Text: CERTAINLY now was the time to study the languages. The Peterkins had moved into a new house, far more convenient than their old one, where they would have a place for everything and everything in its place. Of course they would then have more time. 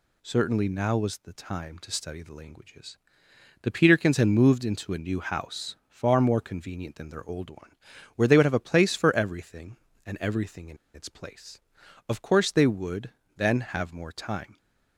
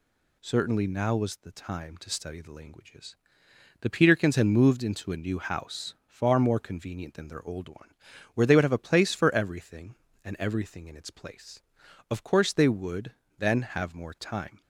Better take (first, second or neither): second